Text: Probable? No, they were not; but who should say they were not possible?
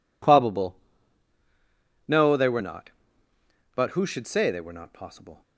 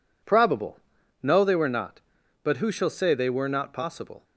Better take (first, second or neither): first